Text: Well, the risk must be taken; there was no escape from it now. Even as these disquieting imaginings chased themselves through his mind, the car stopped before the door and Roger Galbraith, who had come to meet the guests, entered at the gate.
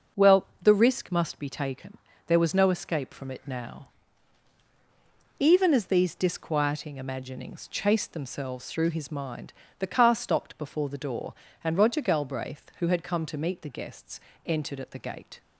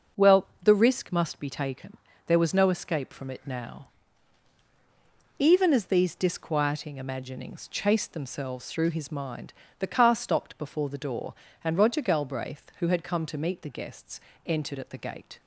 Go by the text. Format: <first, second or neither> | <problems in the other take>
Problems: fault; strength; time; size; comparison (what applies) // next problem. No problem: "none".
neither | none